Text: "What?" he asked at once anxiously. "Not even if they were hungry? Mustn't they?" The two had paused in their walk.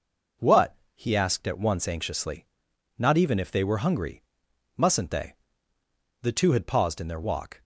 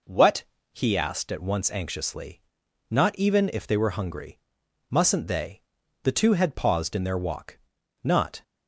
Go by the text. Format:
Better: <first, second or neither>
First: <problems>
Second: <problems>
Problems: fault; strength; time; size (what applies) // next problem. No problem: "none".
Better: first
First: none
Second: goes on to say "Not"; slight; from 8.0 s on; 0.40 s long